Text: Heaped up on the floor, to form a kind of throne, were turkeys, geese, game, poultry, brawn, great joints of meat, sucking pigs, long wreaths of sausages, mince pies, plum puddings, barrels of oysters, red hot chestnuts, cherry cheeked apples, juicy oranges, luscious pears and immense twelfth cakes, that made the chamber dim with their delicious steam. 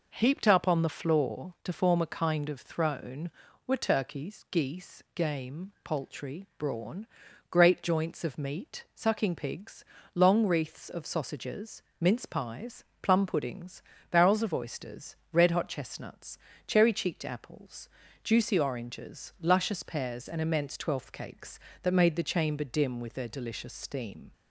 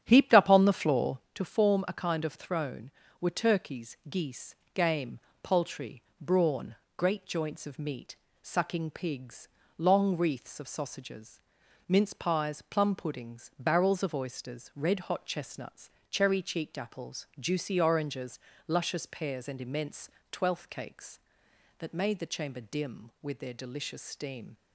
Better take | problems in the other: first | starts louder than the rest; strong; until 1.2 s; 9.5 dB // pauses between "immense" and "twelfth"; slight; at 20.0 s; 0.20 s long

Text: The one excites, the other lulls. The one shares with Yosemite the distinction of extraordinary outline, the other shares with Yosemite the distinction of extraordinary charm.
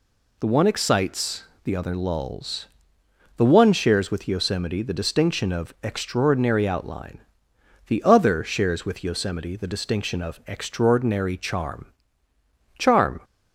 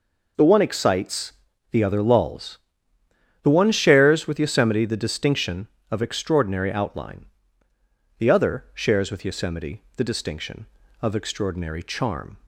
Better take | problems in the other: second | says "charm" twice; at 12.7 s

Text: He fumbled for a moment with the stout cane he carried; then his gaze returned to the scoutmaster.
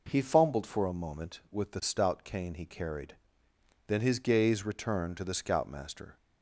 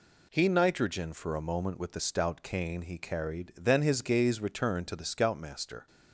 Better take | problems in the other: first | says "nitrogen" for "fumbled"; at 0.4 s

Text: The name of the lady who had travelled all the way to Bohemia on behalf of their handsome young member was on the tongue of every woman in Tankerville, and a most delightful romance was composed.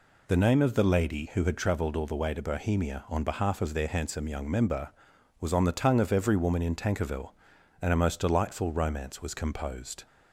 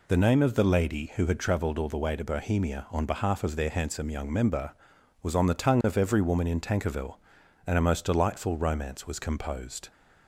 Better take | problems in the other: neither | none

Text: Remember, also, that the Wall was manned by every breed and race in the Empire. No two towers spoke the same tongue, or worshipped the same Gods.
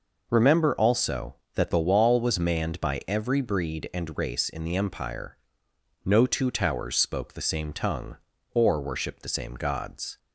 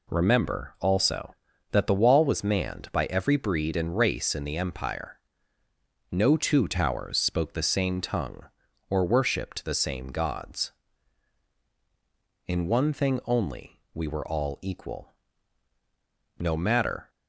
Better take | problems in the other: first | goes on to say "In one thing only we were all equal No matter"; strong; from 12.4 s on; 4.6 s long

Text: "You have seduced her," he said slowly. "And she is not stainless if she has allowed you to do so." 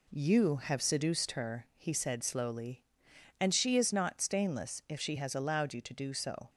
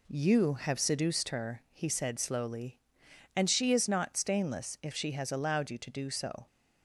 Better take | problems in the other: neither | none

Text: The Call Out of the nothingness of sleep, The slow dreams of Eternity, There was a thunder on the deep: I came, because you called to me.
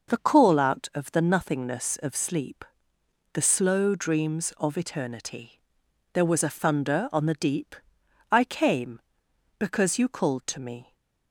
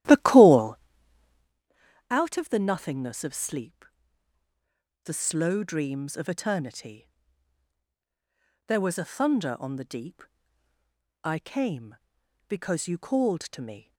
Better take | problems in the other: first | starts louder than the rest; strong; until 1.7 s; 13 dB // pauses between "Call" and "Out"; strong; at 0.7 s; 1.3 s long

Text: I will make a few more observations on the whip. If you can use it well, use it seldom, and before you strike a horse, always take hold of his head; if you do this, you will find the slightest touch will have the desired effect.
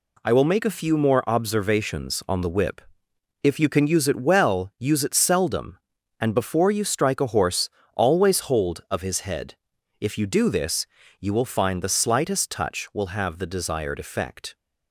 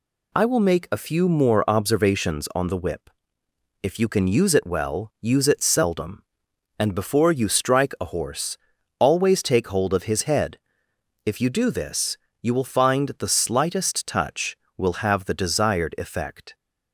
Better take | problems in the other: second | skips "take"; at 8.3 s

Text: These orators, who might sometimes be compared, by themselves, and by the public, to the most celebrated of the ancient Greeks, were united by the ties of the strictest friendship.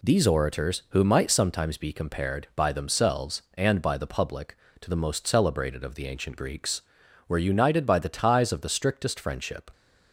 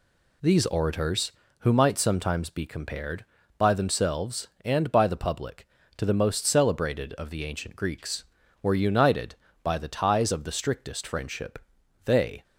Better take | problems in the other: first | goes on to say "They"; slight; from 12.0 s on; 0.38 s long

